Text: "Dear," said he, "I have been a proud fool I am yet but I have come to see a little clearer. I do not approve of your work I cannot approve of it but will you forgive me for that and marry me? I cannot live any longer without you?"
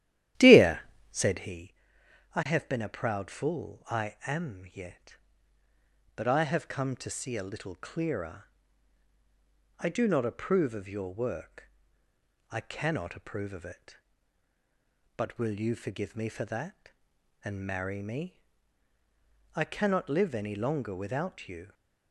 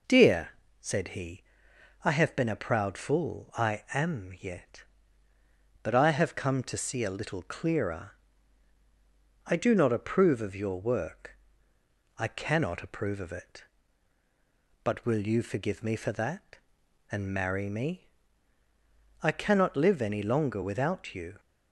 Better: second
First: starts louder than the rest; strong; until 1.6 s; 12.5 dB // pauses between "work" and "I"; noticeable; at 11.7 s; 0.80 s long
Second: pauses between "work" and "I"; noticeable; at 11.3 s; 0.80 s long

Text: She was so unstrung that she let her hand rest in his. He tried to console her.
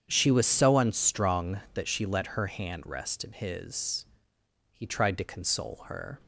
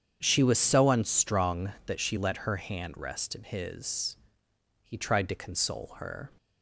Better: neither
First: starts louder than the rest; strong; until 1.0 s; 8 dB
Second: starts louder than the rest; strong; until 1.2 s; 8 dB

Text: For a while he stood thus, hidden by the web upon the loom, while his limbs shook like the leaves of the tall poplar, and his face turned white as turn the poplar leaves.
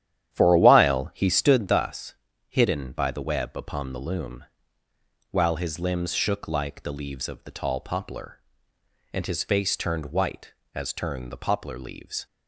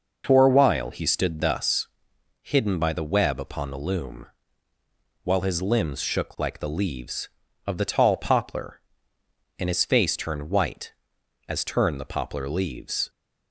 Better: second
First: starts louder than the rest; strong; until 1.7 s; 10.5 dB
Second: none

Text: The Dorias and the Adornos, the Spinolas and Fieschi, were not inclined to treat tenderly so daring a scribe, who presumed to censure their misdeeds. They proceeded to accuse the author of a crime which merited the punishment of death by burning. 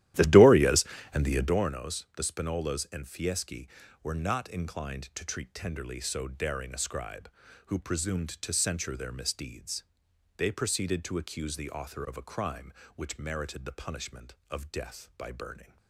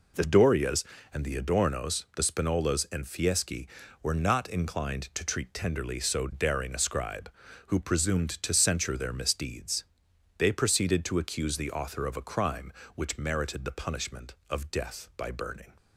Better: second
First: starts louder than the rest; strong; until 1.6 s; 13.5 dB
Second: none

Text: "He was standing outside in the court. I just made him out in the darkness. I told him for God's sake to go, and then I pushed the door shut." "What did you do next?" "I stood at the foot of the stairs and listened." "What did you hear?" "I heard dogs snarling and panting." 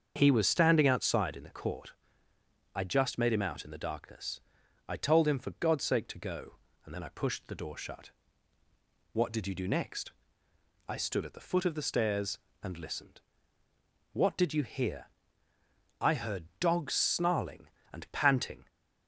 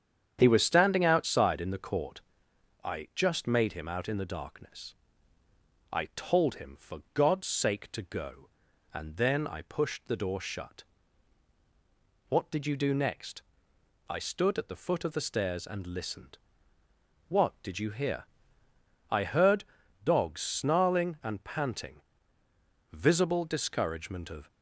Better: first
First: starts louder than the rest; until 1.1 s; 7 dB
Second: starts louder than the rest; strong; until 1.4 s; 8.5 dB // pauses between "heard" and "dogs"; at 19.6 s; 0.38 s long // goes on to say "Visible discouragement of"; from 22.9 s on; 1.5 s long

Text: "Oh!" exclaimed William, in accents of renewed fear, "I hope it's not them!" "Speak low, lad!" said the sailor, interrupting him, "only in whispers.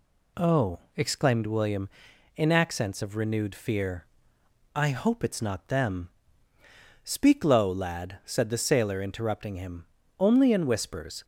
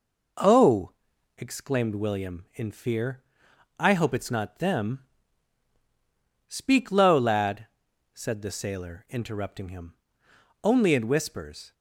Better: first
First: none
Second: skips "accents of renewed"; at 2.7 s

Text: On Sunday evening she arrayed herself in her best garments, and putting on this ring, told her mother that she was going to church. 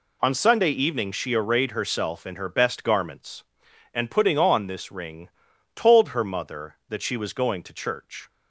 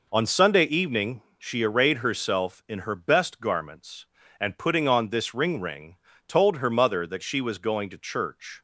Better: first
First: none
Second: pauses between "evening" and "she"; slight; at 1.2 s; 0.16 s long // says "ring" twice; at 5.5 s

